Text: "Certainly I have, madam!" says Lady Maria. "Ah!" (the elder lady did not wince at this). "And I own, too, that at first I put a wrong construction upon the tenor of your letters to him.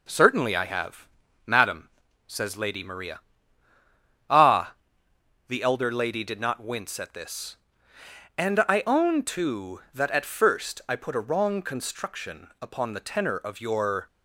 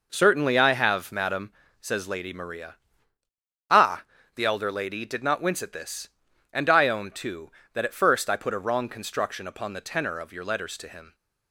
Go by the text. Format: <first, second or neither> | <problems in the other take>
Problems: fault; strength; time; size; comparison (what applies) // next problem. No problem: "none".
second | stops before "letters to him"; at 14.0 s